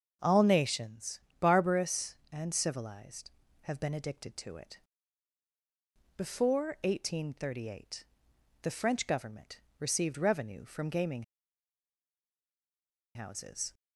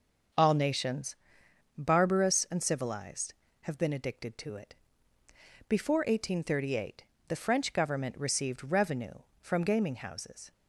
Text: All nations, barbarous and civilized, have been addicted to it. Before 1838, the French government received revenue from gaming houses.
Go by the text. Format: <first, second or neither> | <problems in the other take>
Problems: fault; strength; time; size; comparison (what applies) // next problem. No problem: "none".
second | starts louder than the rest; until 1.2 s; 6.5 dB // pauses between "government" and "received"; slight; at 9.6 s; 0.18 s long // pauses between "gaming" and "houses"; strong; at 11.2 s; 1.9 s long